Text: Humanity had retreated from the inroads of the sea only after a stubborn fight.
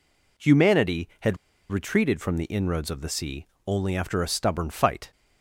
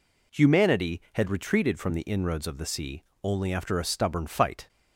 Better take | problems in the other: second | pauses between "had" and "retreated"; slight; at 1.3 s; 0.32 s long // pauses between "sea" and "only"; slight; at 3.4 s; 0.20 s long; slight in the second

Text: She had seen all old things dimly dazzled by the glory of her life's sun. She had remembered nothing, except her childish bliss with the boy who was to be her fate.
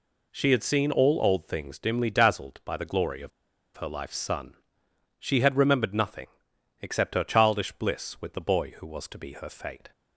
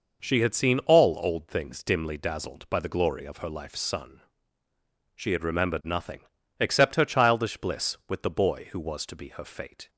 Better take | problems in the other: second | pauses between "of" and "her"; noticeable; at 3.3 s; 0.47 s long

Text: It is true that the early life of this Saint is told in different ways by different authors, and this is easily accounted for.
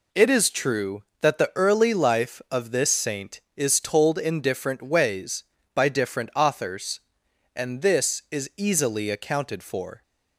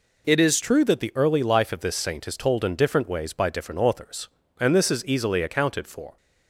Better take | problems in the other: first | changes voice at "true"; from 0.6 s on; 5.5 s long

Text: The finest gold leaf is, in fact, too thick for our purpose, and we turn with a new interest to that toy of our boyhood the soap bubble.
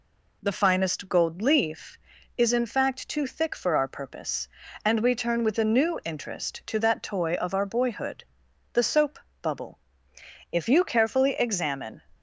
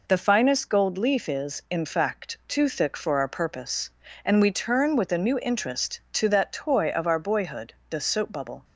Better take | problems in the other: second | pauses between "boyhood" and "the"; noticeable; at 8.2 s; 0.48 s long; slight in the second // pauses between "soap" and "bubble"; slight; at 9.1 s; 0.22 s long // goes on to say "If you carefully examine"; from 10.4 s on; 1.5 s long

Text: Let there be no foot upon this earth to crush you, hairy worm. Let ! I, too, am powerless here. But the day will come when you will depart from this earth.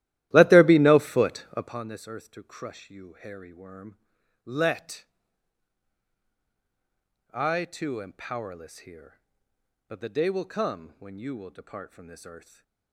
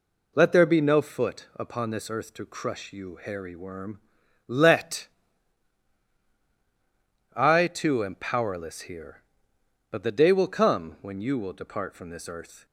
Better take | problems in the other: second | starts louder than the rest; strong; until 1.8 s; 14.5 dB // stays silent after the last word; slight; from 12.3 s on; 0.6 s long

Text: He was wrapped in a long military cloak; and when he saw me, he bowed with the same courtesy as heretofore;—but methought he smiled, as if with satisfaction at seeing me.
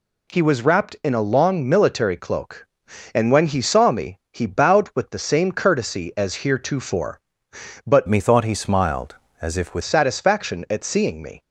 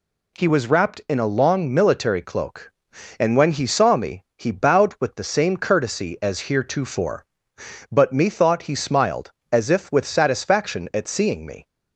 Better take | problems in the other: second | changes voice from "methought" to "with"; from 8.0 to 9.8 s; 1.8 s long

